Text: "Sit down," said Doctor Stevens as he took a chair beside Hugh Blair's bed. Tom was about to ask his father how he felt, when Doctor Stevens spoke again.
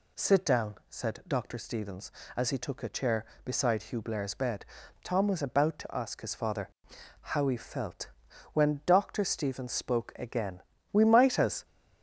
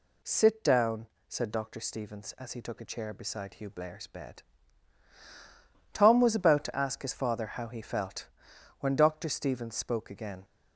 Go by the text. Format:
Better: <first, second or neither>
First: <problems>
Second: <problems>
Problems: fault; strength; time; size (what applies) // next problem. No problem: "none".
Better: second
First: pauses between "father" and "how"; noticeable; at 6.6 s; 0.52 s long // goes on to say "We might as"; noticeable; from 10.9 s on; 0.72 s long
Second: none